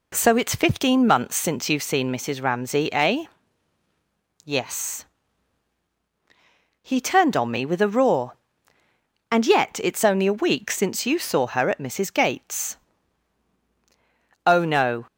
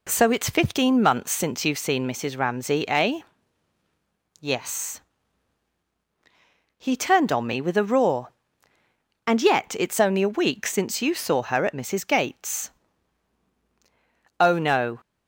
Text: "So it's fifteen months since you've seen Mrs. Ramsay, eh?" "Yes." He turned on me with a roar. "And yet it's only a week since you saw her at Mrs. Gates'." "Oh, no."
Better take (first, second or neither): neither